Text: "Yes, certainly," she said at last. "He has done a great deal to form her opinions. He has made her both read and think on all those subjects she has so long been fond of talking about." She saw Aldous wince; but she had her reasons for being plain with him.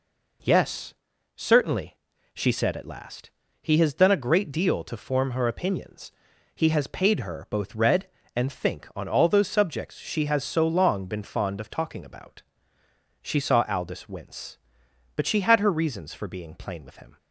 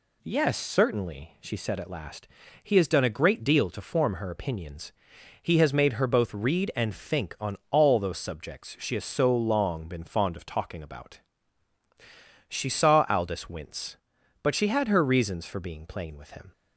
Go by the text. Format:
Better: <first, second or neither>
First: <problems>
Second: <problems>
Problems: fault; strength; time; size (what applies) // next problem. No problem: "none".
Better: second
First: says "paid" for "made"; at 6.8 s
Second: none